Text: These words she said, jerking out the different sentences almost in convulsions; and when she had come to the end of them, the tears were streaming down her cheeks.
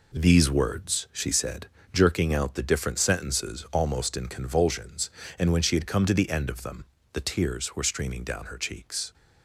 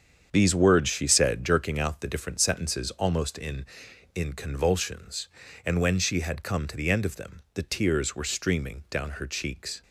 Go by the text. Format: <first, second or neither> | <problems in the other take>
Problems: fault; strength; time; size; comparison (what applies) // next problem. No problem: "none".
first | starts louder than the rest; strong; until 1.3 s; 7.5 dB // says "in" twice; at 4.1 s